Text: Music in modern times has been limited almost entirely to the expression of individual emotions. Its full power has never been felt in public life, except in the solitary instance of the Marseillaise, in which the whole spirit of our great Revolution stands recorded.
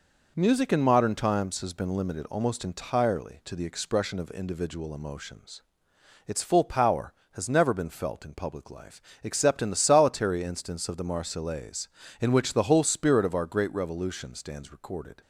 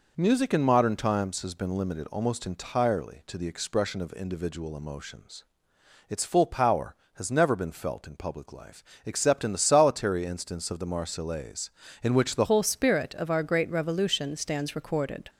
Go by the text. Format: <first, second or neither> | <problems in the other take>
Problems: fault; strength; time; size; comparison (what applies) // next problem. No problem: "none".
first | changes voice at "whole"; from 12.4 s on; 2.8 s long